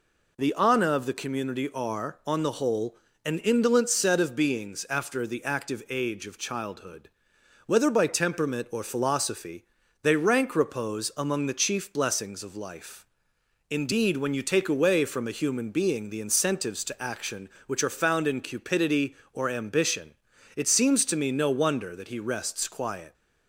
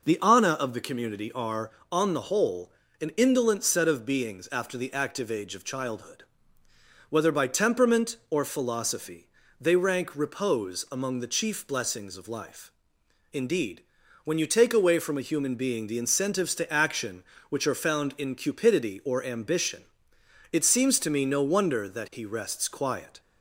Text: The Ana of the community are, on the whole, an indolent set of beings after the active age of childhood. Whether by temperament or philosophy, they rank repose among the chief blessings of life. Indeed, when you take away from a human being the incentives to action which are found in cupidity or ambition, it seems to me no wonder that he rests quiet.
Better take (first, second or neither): neither